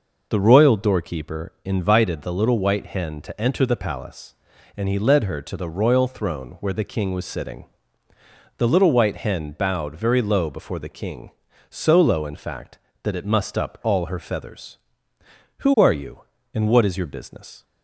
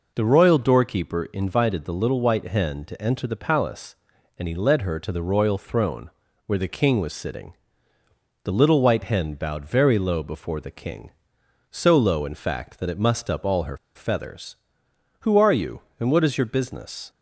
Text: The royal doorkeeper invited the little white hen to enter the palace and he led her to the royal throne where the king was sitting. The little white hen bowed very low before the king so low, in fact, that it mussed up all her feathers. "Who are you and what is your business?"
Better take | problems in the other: first | pauses between "throne" and "where"; slight; at 6.1 s; 0.34 s long // pauses between "her" and "feathers"; slight; at 13.7 s; 0.17 s long

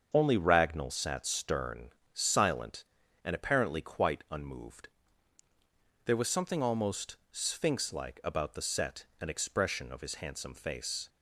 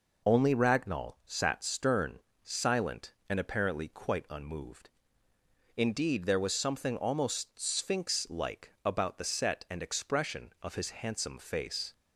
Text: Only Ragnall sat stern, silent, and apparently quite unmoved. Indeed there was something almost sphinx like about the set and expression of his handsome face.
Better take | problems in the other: second | starts louder than the rest; until 1.1 s; 7 dB // skips "Indeed"; at 5.4 s

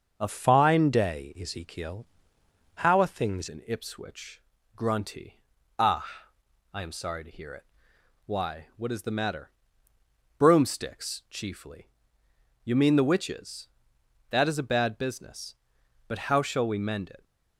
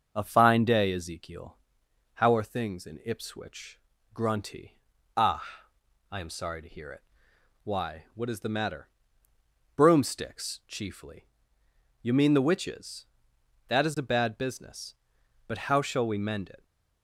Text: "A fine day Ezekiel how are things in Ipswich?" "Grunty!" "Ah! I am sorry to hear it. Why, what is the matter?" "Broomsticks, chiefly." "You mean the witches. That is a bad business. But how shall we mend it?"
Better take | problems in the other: second | starts louder than the rest; until 1.1 s; 6.5 dB; also in the second // changes voice from "fine" to "things"; from 0.2 to 3.4 s; 3.2 s long // pauses between "Ezekiel" and "how"; noticeable; at 2.0 s; 0.68 s long; noticeable in the second

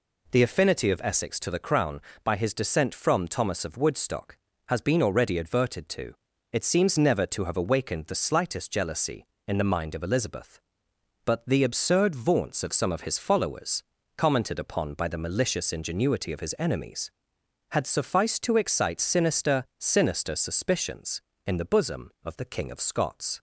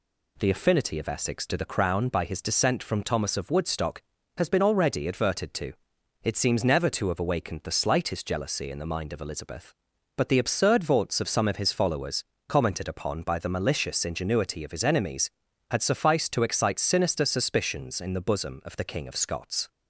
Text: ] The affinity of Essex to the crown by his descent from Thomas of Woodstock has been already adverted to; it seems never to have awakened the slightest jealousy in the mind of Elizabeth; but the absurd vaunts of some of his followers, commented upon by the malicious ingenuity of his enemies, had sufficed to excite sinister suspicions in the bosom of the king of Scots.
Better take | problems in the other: second | says "sinister" twice; at 19.7 s

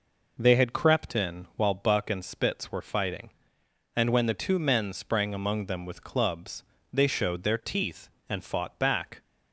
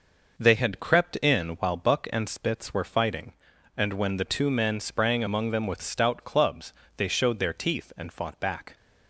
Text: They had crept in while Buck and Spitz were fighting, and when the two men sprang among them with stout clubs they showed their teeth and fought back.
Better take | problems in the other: second | skips "stout"; at 6.0 s // pauses between "clubs" and "they"; slight; at 6.6 s; 0.30 s long; slight in the second

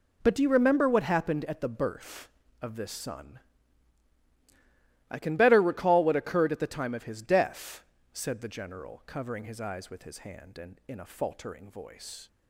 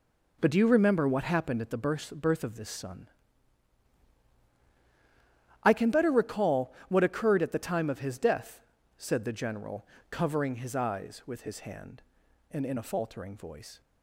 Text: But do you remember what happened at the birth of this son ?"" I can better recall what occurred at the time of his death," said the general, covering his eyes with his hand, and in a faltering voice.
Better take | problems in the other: first | says "birth" twice; at 2.1 s

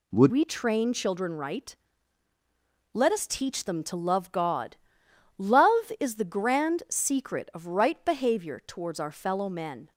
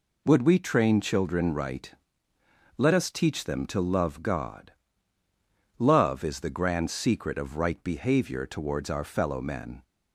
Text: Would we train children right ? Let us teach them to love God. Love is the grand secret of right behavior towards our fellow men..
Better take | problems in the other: second | changes voice at "we"; from 0.2 s on; 9.7 s long

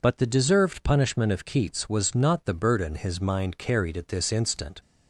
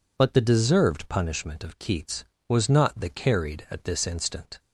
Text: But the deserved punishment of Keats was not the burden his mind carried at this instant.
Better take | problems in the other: first | skips "burden his mind"; at 3.1 s

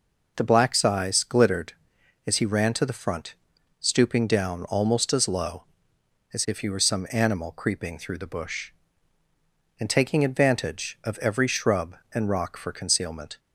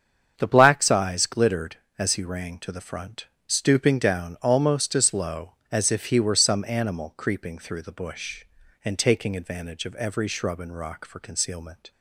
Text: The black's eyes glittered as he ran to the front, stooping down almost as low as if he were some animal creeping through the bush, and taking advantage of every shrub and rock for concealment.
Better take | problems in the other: first | starts louder than the rest; strong; until 1.3 s; 7.5 dB // says "rang" for "ran"; at 2.2 s

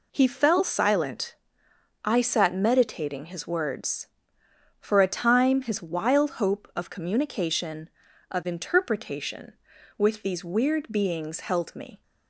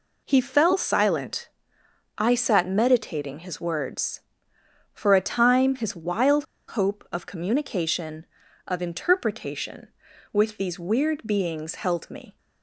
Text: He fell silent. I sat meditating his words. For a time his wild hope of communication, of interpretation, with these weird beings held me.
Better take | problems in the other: first | pauses between "wild" and "hope"; slight; at 6.4 s; 0.23 s long

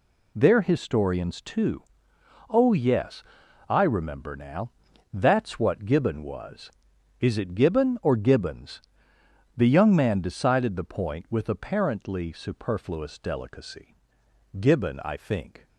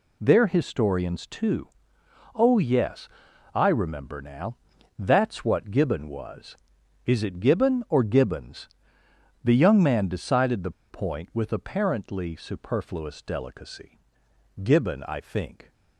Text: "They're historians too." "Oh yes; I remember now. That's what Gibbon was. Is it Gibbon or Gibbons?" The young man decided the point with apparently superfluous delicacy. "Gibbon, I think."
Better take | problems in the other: first | pauses between "the" and "point"; slight; at 10.7 s; 0.19 s long

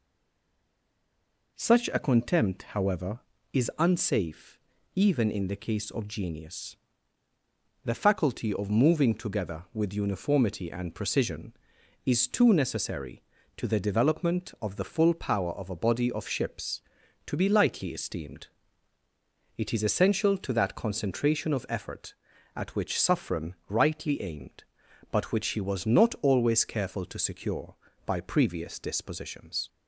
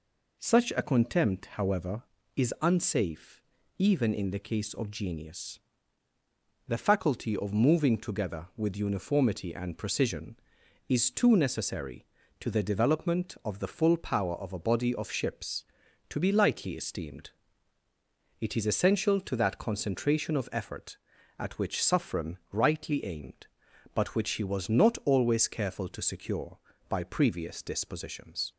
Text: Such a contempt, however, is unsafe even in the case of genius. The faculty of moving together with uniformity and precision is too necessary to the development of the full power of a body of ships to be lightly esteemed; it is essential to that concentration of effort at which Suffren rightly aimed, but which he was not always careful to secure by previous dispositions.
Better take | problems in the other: second | stays silent before the first word; noticeable; until 1.5 s; 1.5 s long // pauses between "unsafe" and "even"; slight; at 4.5 s; 0.36 s long; slight in the second

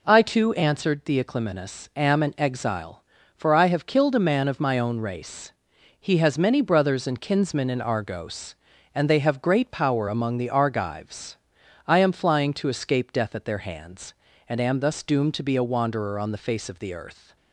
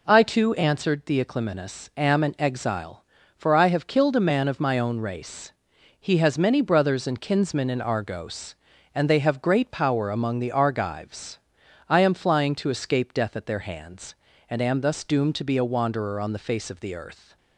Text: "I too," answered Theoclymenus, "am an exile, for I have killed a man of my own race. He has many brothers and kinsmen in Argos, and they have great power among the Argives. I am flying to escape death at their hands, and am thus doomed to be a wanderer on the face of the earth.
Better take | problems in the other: neither | none

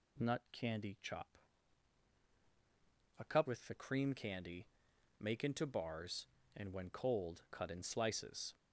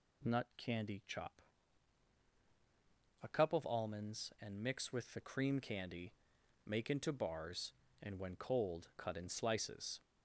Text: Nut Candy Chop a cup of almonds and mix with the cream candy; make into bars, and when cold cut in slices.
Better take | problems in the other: second | pauses between "Chop" and "a"; strong; at 1.2 s; 1.9 s long; strong in the second // skips "of almonds and mix"; at 3.4 s

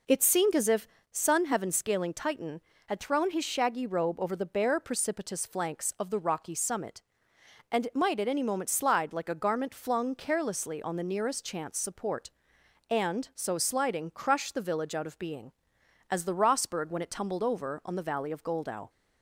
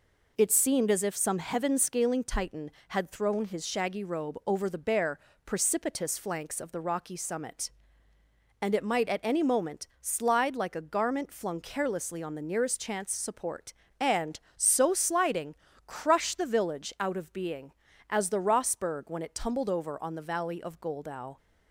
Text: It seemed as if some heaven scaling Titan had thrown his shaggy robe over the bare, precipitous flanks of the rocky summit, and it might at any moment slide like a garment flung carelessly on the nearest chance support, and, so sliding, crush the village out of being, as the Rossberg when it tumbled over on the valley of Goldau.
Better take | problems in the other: second | says "sun" for "some"; at 1.1 s

